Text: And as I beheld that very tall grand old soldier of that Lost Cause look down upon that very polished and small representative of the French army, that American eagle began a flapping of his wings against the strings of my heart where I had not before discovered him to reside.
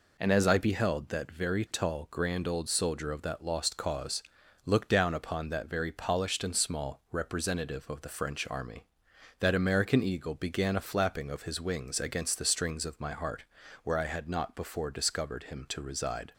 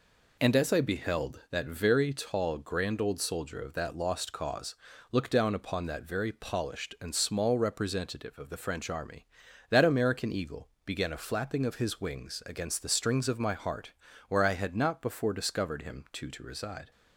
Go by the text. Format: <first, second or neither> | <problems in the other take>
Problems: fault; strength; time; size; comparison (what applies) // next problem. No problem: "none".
first | pauses between "Cause" and "look"; slight; at 4.7 s; 0.36 s long; also in the first // pauses between "eagle" and "began"; slight; at 10.6 s; 0.16 s long // pauses between "heart" and "where"; slight; at 13.9 s; 0.36 s long; also in the first // says "to" twice; at 16.3 s